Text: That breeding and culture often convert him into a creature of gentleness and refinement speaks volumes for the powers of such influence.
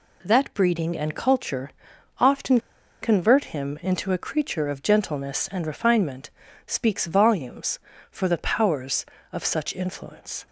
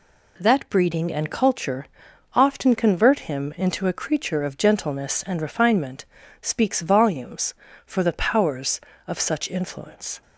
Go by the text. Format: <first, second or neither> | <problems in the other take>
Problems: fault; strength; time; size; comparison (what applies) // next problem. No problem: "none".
second | pauses between "culture" and "often"; noticeable; at 1.7 s; 0.48 s long; noticeable in the second // pauses between "often" and "convert"; at 2.5 s; 0.42 s long // pauses between "refinement" and "speaks"; at 6.3 s; 0.38 s long; also in the second